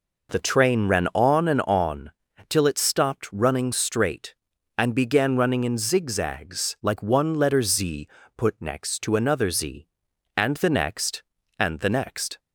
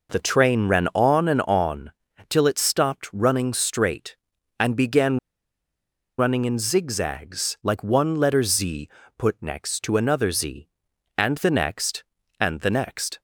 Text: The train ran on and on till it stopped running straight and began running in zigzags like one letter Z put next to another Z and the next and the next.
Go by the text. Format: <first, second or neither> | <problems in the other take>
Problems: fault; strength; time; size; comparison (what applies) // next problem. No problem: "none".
first | pauses between "on" and "till"; slight; at 1.9 s; 0.36 s long; slight in the first // pauses between "began" and "running"; at 5.1 s; 0.99 s long // pauses between "Z" and "put"; slight; at 8.8 s; 0.30 s long; slight in the first